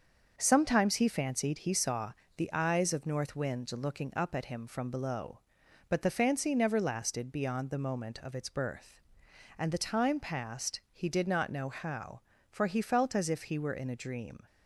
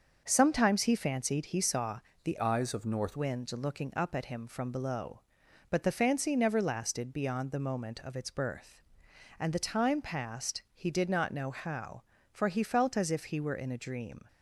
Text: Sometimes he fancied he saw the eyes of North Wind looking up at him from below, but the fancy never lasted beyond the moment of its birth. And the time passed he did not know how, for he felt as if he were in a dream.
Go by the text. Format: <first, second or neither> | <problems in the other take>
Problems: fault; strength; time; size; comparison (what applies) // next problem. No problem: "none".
first | starts louder than the rest; until 1.2 s; 6.5 dB; also in the first // pauses between "saw" and "the"; slight; at 1.9 s; 0.24 s long; slight in the first // changes voice from "eyes" to "North"; from 2.4 to 3.1 s; 0.7 s long